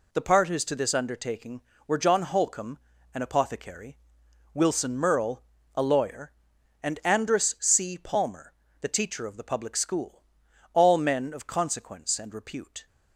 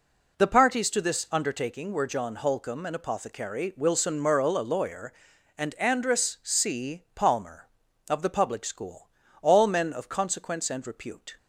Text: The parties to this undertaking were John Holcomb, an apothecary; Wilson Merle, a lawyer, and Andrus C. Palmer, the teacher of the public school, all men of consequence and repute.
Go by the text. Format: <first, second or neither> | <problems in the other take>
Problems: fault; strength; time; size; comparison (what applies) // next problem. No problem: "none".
first | skips "the teacher"; at 7.8 s